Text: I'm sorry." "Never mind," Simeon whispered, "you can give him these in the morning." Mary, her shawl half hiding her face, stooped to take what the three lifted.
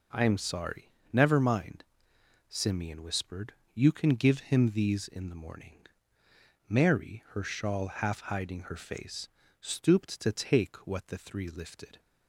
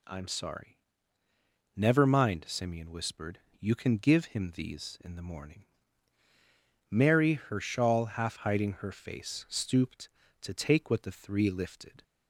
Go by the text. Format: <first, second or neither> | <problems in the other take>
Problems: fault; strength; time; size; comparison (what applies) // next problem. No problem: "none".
neither | none